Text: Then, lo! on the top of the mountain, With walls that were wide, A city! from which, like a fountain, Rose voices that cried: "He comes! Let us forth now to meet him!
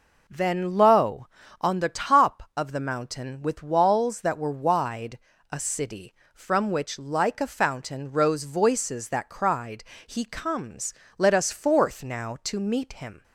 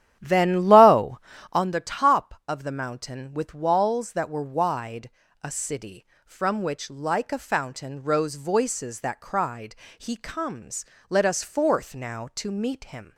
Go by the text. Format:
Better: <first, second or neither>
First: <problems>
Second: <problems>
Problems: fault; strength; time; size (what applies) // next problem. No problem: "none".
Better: first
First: none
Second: starts louder than the rest; strong; until 1.7 s; 11 dB